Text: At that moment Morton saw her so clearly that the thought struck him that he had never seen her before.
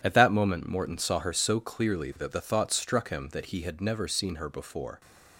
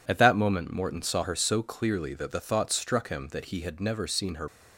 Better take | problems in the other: first | stops before "before"; at 4.4 s

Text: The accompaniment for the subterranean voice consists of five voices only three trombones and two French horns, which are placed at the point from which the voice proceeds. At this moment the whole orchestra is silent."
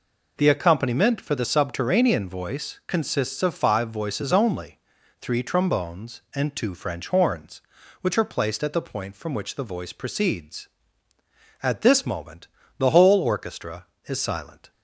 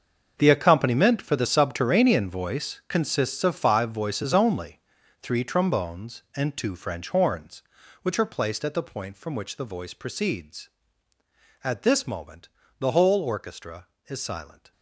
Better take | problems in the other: first | gets quieter; strong; throughout; 14.5 dB // pauses between "only" and "three"; at 4.7 s; 0.42 s long; also in the first // pauses between "moment" and "the"; slight; at 12.4 s; 0.30 s long; slight in the first

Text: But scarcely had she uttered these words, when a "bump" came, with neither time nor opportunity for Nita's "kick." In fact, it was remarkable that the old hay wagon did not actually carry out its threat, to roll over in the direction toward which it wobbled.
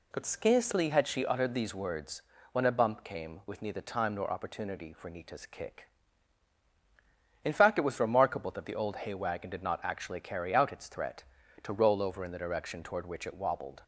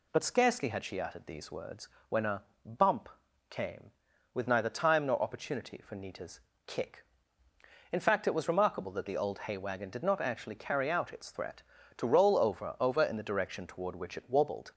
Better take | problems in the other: first | pauses between "a" and "bump"; slight; at 2.4 s; 0.22 s long // pauses between "bump" and "came"; at 3.1 s; 0.40 s long // pauses between "Nita's" and "kick"; slight; at 6.4 s; 0.24 s long // says "over" twice; at 12.8 s

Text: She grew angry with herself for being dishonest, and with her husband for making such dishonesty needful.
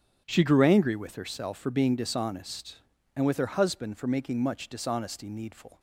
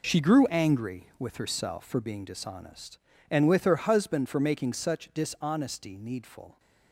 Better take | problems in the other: second | starts louder than the rest; strong; until 1.2 s; 8.5 dB // says "much" for "such"; at 4.3 s

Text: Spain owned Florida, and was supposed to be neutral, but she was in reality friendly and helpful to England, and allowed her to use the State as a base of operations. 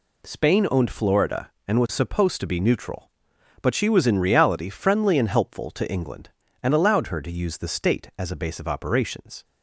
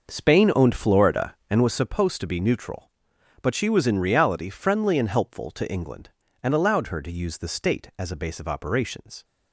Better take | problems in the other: first | starts louder than the rest; noticeable; until 1.8 s; 6 dB

